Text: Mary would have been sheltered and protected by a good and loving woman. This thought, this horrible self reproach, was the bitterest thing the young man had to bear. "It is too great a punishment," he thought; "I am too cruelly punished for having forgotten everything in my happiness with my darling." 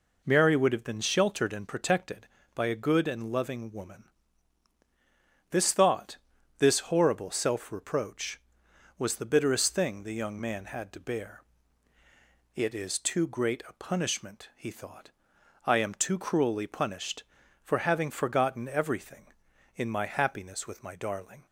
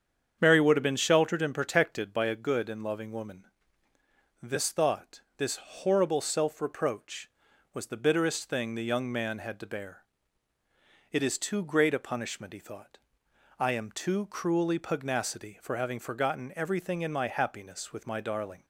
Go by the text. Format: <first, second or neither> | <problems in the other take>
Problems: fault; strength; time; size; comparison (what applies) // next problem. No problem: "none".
first | starts louder than the rest; strong; until 1.4 s; 7.5 dB // says "pugnacity" for "punished"; at 14.7 s